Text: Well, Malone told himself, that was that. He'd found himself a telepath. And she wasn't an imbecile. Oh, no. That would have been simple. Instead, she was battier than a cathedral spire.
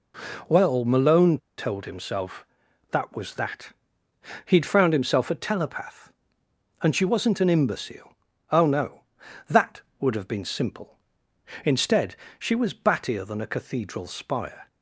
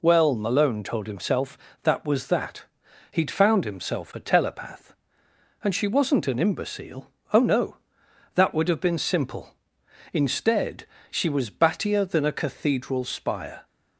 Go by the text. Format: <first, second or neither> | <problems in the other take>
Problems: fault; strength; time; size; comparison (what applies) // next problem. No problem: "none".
second | pauses between "Malone" and "told"; slight; at 1.3 s; 0.20 s long